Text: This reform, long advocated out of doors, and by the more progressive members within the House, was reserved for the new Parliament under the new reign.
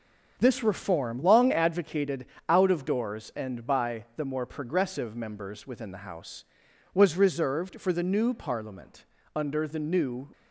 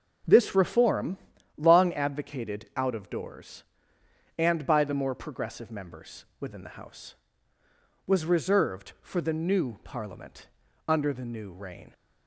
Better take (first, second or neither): second